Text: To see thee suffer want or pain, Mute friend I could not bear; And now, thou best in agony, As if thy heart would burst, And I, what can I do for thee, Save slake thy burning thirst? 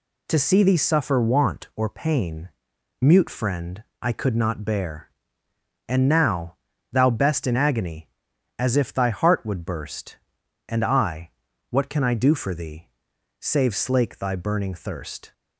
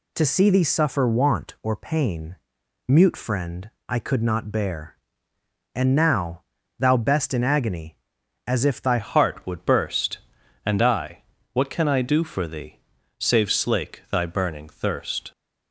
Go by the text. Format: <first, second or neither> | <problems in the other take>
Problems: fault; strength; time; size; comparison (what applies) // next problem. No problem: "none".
first | pauses between "friend" and "I"; slight; at 3.6 s; 0.18 s long; slight in the first // changes voice at "heart"; from 8.9 s on; 6.4 s long